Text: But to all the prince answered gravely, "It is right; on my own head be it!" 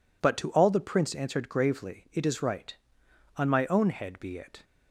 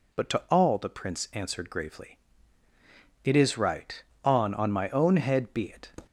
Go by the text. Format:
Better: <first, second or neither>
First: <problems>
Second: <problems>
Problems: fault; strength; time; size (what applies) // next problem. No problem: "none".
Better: first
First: none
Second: says "on" twice; at 4.5 s